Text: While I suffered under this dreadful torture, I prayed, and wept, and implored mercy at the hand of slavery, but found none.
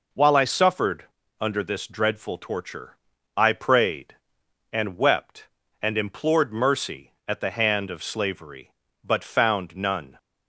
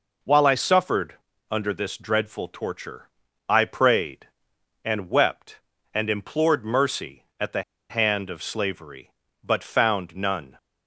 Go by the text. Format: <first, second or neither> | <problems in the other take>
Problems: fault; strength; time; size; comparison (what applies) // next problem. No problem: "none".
first | pauses between "suffered" and "under"; slight; at 1.1 s; 0.34 s long; slight in the first // pauses between "the" and "hand"; slight; at 7.6 s; 0.26 s long